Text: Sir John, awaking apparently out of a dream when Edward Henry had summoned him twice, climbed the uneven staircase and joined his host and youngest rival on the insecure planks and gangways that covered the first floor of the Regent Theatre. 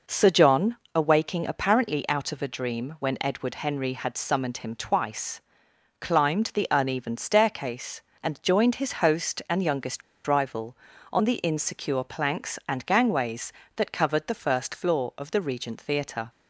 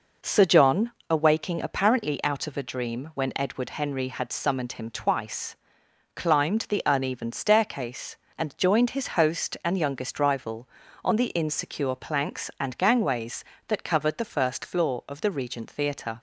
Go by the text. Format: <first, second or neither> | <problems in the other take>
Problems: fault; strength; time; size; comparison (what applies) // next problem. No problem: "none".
second | pauses between "youngest" and "rival"; slight; at 10.0 s; 0.26 s long